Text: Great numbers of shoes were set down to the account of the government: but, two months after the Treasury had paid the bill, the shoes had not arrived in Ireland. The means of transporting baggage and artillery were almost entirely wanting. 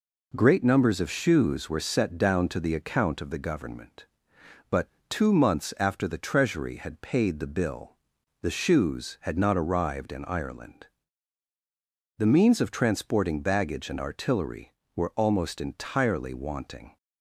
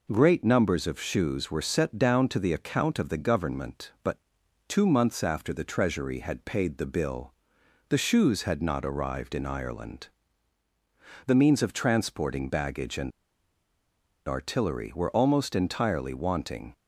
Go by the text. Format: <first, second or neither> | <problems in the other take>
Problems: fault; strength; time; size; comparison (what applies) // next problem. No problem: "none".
first | pauses between "and" and "artillery"; at 13.1 s; 1.1 s long